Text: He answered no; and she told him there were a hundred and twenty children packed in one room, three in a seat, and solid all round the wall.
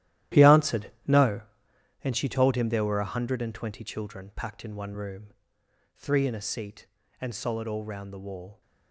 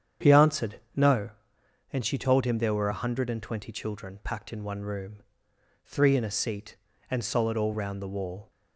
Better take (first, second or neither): second